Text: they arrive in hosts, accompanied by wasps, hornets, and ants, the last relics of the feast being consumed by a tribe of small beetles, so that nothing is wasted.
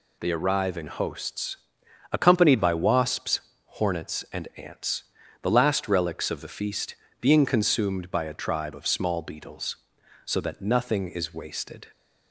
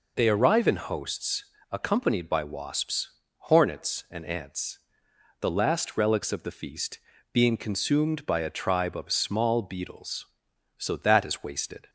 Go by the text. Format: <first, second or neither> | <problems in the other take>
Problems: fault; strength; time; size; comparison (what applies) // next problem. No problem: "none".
first | pauses between "feast" and "being"; slight; at 6.9 s; 0.34 s long; slight in the first // skips "nothing"; at 11.2 s